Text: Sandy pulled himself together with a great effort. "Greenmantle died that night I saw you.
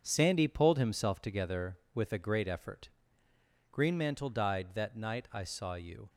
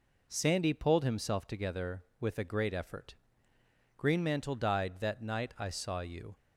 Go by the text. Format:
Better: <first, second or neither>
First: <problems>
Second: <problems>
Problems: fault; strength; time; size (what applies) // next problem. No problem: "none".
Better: second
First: gets quieter; strong; throughout; 8 dB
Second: none